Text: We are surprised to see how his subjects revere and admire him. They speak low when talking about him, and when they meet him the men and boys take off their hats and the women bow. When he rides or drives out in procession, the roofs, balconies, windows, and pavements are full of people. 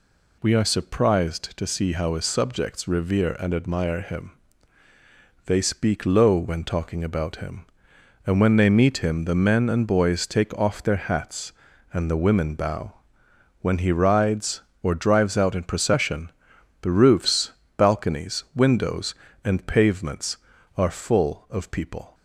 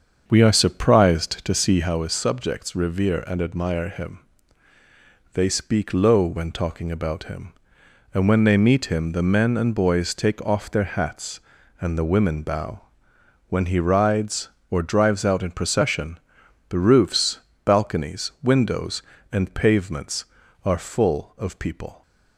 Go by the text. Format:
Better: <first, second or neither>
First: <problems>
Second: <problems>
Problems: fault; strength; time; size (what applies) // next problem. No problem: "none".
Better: first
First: none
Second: starts louder than the rest; until 1.9 s; 7 dB